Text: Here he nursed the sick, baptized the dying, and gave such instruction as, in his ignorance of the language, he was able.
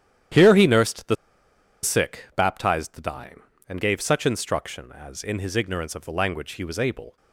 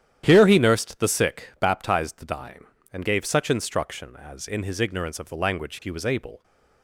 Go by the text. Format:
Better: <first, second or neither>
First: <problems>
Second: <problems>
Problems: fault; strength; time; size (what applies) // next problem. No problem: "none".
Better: second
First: starts louder than the rest; strong; until 2.0 s; 10.5 dB // pauses between "the" and "sick"; noticeable; at 1.1 s; 0.68 s long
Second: starts louder than the rest; strong; until 1.2 s; 10.5 dB